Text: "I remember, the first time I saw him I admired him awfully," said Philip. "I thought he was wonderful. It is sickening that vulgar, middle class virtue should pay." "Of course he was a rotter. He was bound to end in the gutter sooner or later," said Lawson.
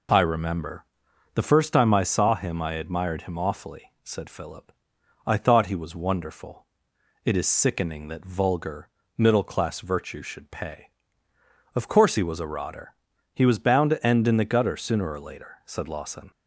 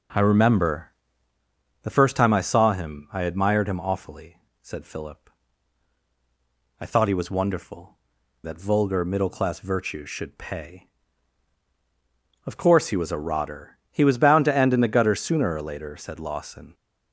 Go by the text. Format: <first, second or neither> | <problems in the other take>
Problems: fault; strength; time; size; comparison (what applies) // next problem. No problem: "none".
first | skips "It is sickening"; at 8.2 s